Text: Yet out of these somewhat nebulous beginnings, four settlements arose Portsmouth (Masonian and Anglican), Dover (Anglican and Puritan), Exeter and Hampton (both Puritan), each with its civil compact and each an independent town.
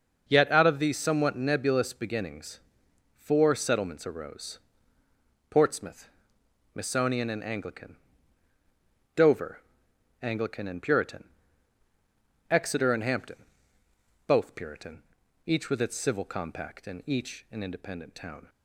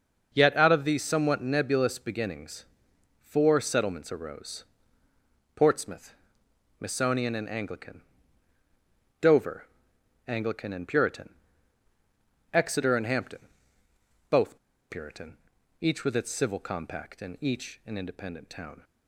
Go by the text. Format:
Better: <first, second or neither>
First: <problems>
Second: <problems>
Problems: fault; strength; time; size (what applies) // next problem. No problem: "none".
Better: first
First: starts louder than the rest; until 1.2 s; 6.5 dB // pauses between "arose" and "Portsmouth"; noticeable; at 4.5 s; 0.92 s long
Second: starts louder than the rest; until 1.3 s; 6.5 dB // pauses between "arose" and "Portsmouth"; noticeable; at 4.6 s; 0.92 s long // pauses between "both" and "Puritan"; slight; at 14.5 s; 0.32 s long